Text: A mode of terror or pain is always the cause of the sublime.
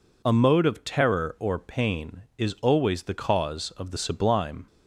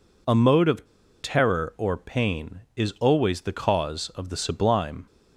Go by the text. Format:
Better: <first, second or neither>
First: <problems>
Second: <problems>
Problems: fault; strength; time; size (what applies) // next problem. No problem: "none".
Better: first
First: none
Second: pauses between "of" and "terror"; slight; at 0.8 s; 0.36 s long